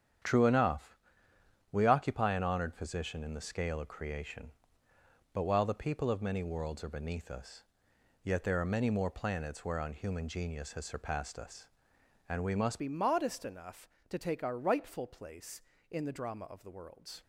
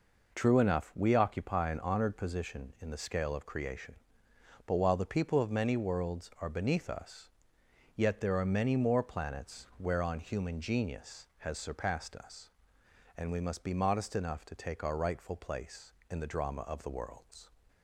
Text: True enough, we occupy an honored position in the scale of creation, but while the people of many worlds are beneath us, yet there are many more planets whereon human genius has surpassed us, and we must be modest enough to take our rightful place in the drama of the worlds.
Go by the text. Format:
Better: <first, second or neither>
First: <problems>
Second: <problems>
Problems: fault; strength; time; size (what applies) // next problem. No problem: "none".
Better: second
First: starts louder than the rest; strong; until 2.0 s; 9 dB // changes voice at "be"; from 12.7 s on; 4.5 s long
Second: none